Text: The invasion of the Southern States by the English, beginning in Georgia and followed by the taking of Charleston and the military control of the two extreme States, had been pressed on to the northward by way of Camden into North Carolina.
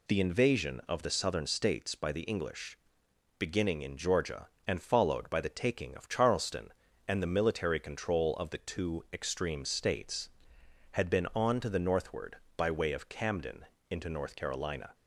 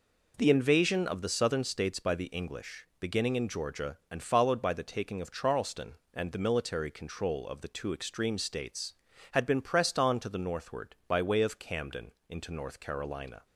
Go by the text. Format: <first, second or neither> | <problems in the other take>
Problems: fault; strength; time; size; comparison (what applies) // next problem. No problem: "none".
second | skips "pressed"; at 11.3 s // pauses between "Camden" and "into"; slight; at 13.6 s; 0.26 s long; slight in the second